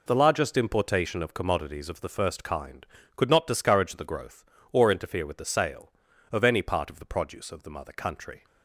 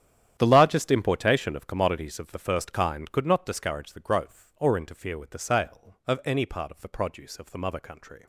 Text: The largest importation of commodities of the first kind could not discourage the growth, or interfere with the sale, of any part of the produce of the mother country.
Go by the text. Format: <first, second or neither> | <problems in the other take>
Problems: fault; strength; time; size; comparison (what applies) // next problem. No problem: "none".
first | gets quieter; strong; throughout; 15.5 dB